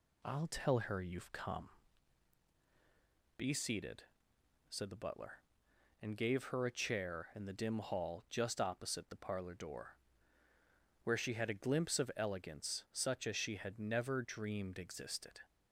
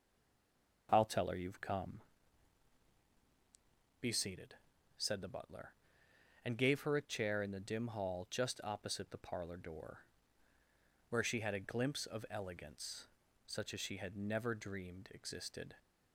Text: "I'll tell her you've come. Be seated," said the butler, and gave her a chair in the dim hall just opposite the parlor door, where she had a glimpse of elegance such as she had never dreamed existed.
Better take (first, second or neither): first